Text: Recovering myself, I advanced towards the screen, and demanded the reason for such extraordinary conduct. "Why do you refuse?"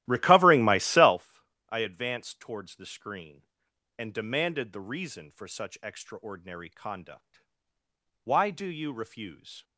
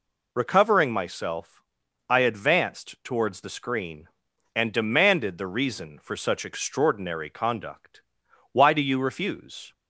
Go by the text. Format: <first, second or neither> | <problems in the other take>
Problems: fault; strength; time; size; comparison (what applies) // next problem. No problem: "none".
second | starts louder than the rest; strong; until 1.3 s; 14.5 dB